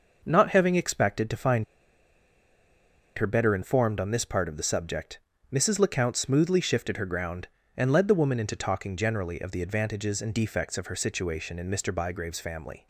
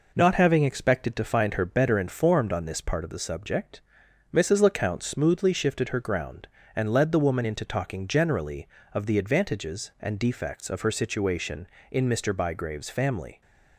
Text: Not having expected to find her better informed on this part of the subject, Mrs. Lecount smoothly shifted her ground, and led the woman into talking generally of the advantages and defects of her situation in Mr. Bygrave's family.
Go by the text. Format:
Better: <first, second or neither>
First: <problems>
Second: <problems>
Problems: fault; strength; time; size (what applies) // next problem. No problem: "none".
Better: second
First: pauses between "find" and "her"; strong; at 1.6 s; 1.5 s long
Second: none